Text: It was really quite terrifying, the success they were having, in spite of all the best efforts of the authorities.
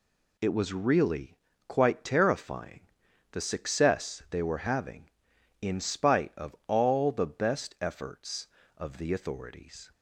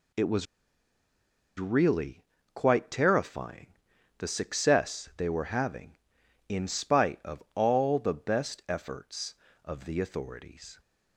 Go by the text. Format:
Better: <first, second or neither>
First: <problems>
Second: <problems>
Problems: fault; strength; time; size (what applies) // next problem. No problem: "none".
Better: first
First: pauses between "really" and "quite"; slight; at 1.3 s; 0.32 s long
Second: pauses between "was" and "really"; at 0.4 s; 1.1 s long // pauses between "really" and "quite"; slight; at 2.2 s; 0.32 s long